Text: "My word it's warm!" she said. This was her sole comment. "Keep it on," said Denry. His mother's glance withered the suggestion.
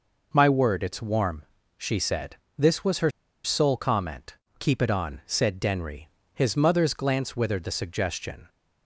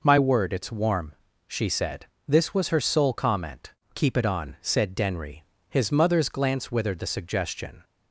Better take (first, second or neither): second